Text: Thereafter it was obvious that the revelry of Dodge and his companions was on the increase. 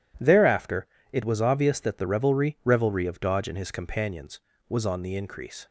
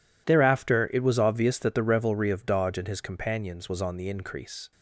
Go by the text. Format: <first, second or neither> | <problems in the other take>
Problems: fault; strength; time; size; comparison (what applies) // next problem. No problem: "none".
second | pauses between "Thereafter" and "it"; slight; at 0.8 s; 0.24 s long // says "revelry" twice; at 2.6 s